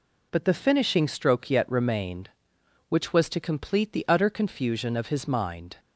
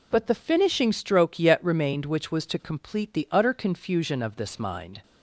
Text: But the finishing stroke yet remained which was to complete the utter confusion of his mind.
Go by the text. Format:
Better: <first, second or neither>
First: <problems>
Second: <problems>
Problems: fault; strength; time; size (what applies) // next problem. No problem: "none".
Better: first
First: none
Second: says "this" for "his"; at 4.3 s